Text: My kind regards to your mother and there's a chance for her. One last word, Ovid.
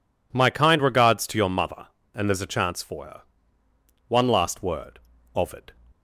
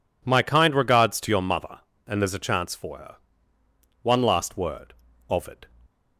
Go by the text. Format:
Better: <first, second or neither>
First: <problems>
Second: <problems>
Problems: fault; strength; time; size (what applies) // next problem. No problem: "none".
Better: neither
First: none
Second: none